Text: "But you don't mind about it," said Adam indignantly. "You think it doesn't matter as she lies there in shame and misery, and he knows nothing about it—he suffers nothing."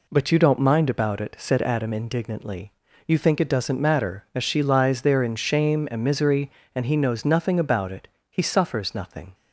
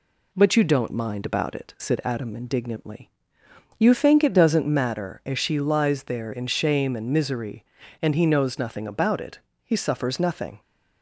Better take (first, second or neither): neither